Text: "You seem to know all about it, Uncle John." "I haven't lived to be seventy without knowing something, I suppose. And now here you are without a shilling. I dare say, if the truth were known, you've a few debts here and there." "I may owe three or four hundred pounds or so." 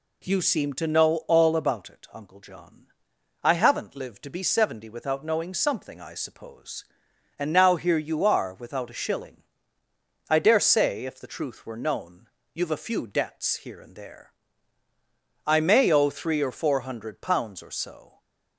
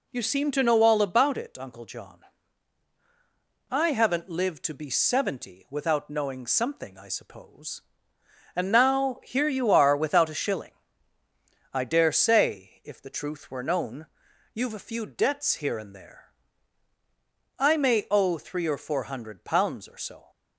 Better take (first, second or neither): neither